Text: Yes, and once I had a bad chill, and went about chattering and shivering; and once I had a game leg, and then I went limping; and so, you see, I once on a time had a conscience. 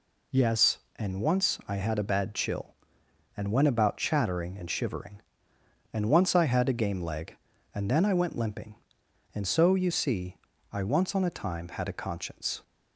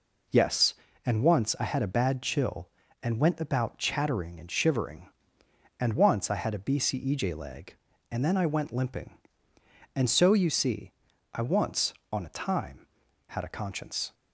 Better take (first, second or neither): first